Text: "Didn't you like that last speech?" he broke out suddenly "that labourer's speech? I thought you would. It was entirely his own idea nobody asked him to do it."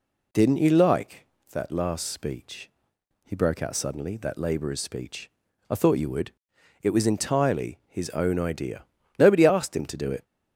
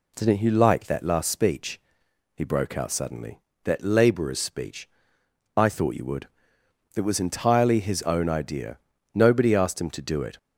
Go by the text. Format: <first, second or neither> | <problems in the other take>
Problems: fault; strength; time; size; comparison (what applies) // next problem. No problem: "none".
neither | pauses between "idea" and "nobody"; slight; the same in both